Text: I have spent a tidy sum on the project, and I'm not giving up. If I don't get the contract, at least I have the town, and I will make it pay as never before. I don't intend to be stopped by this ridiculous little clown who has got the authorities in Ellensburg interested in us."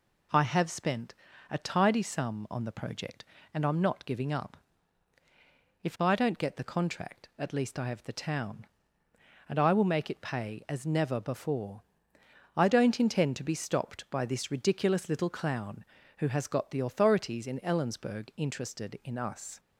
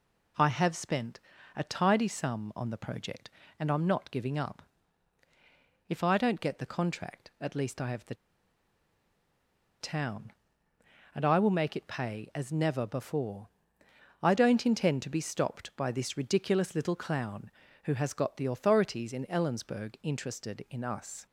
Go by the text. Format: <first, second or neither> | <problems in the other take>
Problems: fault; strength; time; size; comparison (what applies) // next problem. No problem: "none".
first | pauses between "spent" and "a"; slight; at 1.1 s; 0.36 s long; slight in the first // pauses between "the" and "town"; strong; at 8.1 s; 1.6 s long